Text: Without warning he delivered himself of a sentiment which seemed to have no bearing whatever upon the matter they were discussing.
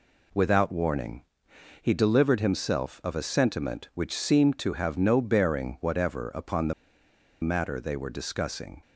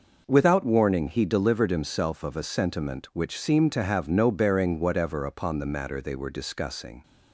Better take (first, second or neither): second